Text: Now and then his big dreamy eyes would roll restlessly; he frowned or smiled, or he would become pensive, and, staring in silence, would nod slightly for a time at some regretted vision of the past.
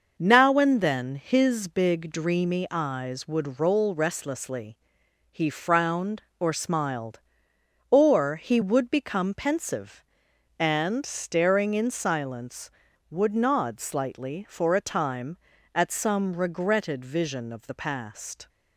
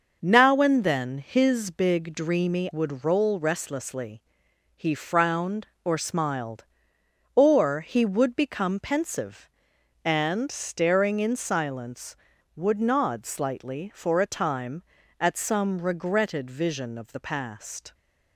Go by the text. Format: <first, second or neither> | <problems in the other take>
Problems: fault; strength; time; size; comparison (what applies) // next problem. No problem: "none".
first | skips "eyes"; at 2.6 s